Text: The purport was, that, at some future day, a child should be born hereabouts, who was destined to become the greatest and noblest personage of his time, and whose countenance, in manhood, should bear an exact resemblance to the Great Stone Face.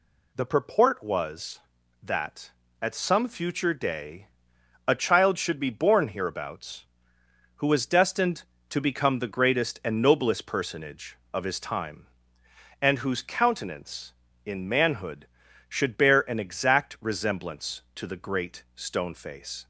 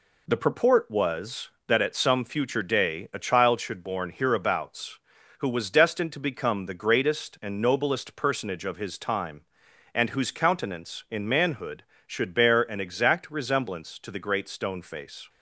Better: first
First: none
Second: skips "be"; at 3.8 s

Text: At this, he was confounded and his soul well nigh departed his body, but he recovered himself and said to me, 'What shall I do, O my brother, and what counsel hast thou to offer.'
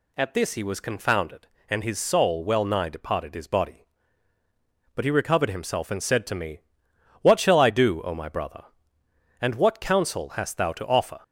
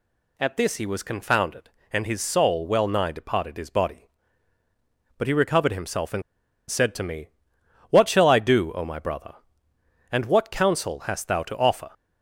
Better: first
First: none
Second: pauses between "and" and "said"; noticeable; at 6.2 s; 0.47 s long

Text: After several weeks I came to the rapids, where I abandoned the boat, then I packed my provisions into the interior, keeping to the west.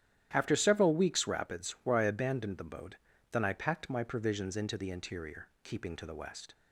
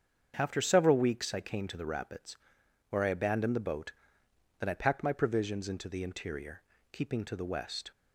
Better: second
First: starts louder than the rest; strong; until 1.3 s; 11.5 dB // skips "I came to the"; at 1.2 s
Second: starts louder than the rest; strong; until 1.3 s; 7 dB

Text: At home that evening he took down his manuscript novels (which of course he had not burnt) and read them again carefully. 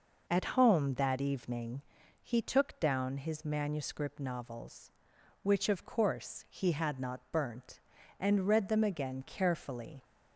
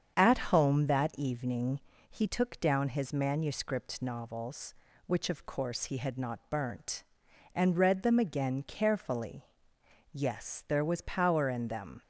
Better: first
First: pauses between "evening" and "he"; at 1.8 s; 0.38 s long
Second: starts louder than the rest; strong; until 1.1 s; 7.5 dB // pauses between "evening" and "he"; slight; at 1.7 s; 0.30 s long // goes on to say "Yes there was power in them"; strong; from 10.1 s on; 1.9 s long

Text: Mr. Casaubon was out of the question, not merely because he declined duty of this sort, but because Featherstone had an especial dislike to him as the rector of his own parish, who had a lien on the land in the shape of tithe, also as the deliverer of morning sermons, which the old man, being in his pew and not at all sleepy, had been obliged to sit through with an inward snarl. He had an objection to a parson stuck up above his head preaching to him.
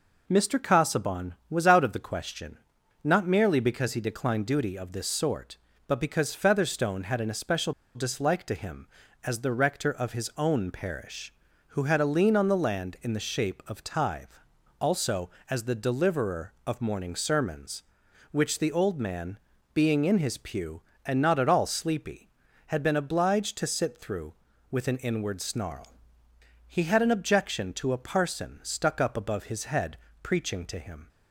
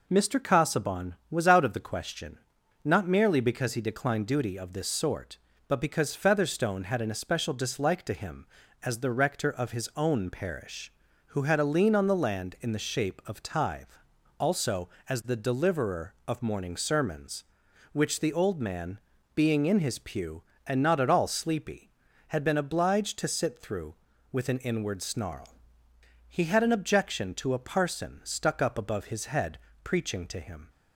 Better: second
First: pauses between "especial" and "dislike"; slight; at 7.7 s; 0.23 s long // pauses between "head" and "preaching"; slight; at 29.9 s; 0.26 s long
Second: pauses between "head" and "preaching"; slight; at 29.5 s; 0.26 s long

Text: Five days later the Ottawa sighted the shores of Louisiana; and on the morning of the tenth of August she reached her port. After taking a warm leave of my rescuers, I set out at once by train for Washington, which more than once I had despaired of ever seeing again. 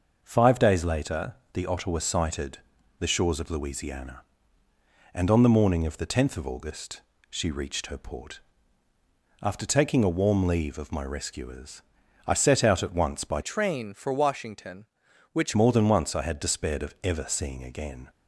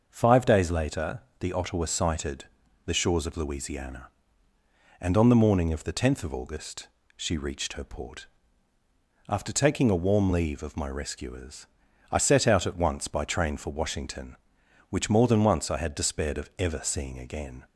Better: second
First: starts louder than the rest; noticeable; until 1.2 s; 6 dB // pauses between "later" and "the"; slight; at 1.3 s; 0.18 s long // pauses between "sighted" and "the"; at 2.5 s; 0.40 s long // pauses between "August" and "she"; slight; at 7.0 s; 0.26 s long // changes voice from "train" to "which"; from 13.4 to 15.5 s; 2.1 s long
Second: starts louder than the rest; noticeable; until 1.0 s; 6 dB // pauses between "later" and "the"; slight; at 1.2 s; 0.18 s long // pauses between "sighted" and "the"; at 2.4 s; 0.40 s long // pauses between "August" and "she"; slight; at 6.8 s; 0.26 s long

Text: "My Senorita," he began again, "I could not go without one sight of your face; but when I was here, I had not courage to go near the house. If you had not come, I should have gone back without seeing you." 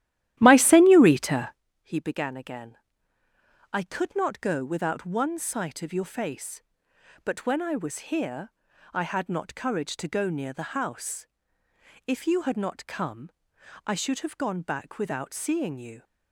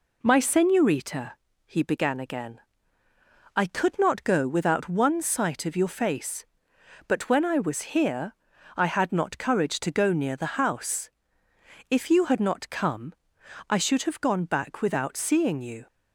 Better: second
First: starts louder than the rest; strong; until 1.6 s; 13.5 dB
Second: none

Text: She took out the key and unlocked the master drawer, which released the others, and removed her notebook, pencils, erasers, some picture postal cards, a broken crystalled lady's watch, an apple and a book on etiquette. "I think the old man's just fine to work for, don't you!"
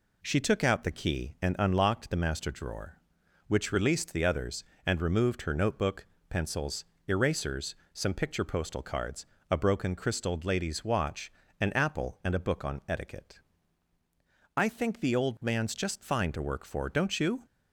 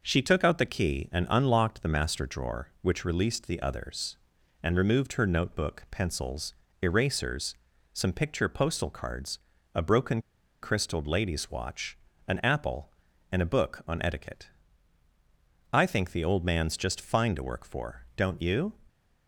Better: first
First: none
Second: pauses between "broken" and "crystalled"; at 10.1 s; 0.43 s long

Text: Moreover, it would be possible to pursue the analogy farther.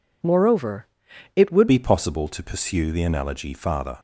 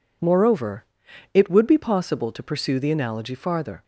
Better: second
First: changes voice at "be"; from 1.6 s on; 2.3 s long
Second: none

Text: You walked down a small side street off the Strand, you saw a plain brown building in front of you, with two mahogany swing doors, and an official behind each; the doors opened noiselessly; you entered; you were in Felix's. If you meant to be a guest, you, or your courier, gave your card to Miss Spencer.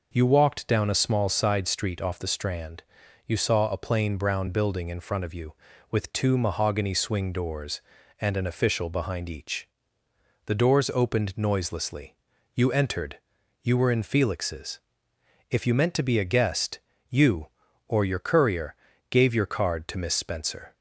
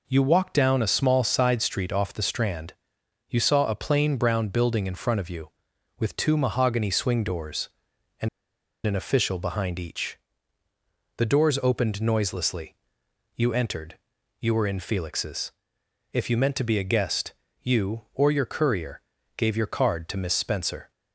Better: first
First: none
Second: pauses between "and" and "an"; noticeable; at 8.2 s; 0.57 s long

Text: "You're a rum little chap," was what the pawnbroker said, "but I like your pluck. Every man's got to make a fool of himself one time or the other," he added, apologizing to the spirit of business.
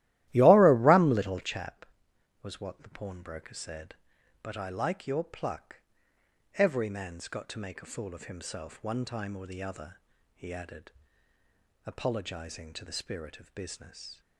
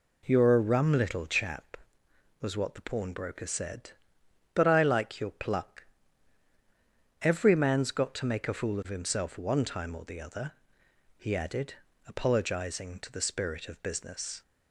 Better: second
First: starts louder than the rest; strong; until 1.6 s; 15 dB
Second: none

